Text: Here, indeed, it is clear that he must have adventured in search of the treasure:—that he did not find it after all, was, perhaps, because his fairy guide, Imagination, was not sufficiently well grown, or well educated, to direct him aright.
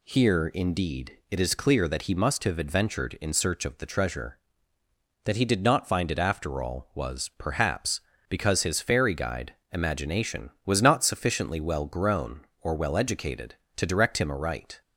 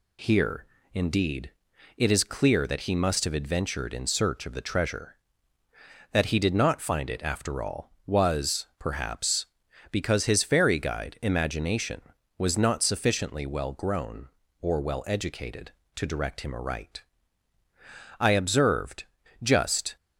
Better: first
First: none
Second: goes on to say "I observed just"; strong; from 18.1 s on; 1.7 s long

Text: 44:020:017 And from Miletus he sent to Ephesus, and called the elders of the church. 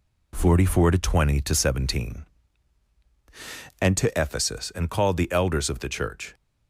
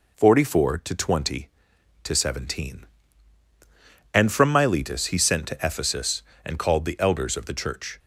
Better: second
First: skips "from Miletus he sent"; at 3.9 s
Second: none

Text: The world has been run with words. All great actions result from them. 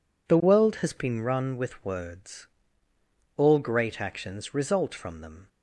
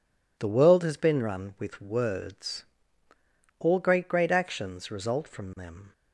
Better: first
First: none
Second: says "great" twice; at 4.0 s

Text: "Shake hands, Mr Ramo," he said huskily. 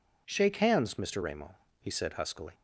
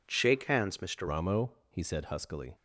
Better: first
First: none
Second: changes voice at "Ramo"; from 1.0 s on; 1.5 s long

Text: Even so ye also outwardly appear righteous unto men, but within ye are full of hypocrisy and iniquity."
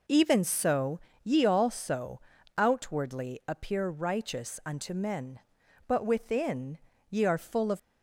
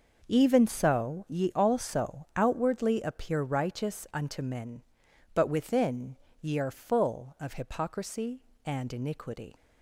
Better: second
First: pauses between "so" and "ye"; slight; at 0.9 s; 0.24 s long // pauses between "also" and "outwardly"; slight; at 2.2 s; 0.36 s long // pauses between "within" and "ye"; slight; at 6.7 s; 0.32 s long // stops before "hypocrisy and iniquity"; at 7.7 s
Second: pauses between "within" and "ye"; slight; at 6.1 s; 0.26 s long

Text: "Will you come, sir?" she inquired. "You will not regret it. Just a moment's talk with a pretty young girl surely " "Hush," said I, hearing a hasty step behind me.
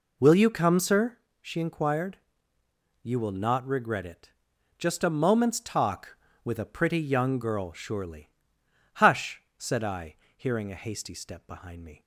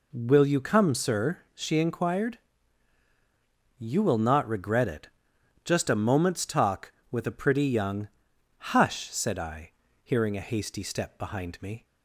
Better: first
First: none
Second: skips "girl surely"; at 8.2 s

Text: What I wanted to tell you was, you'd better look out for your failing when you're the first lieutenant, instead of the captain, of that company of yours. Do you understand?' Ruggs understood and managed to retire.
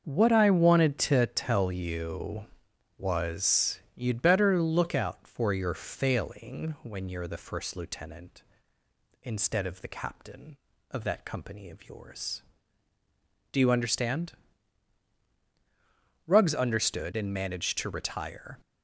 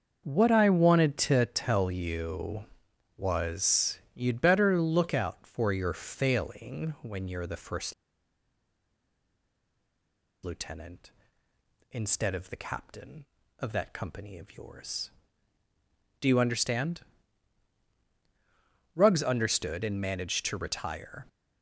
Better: first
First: starts louder than the rest; until 1.0 s; 6.5 dB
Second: starts louder than the rest; until 1.2 s; 6.5 dB // pauses between "first" and "lieutenant"; strong; at 7.9 s; 2.4 s long

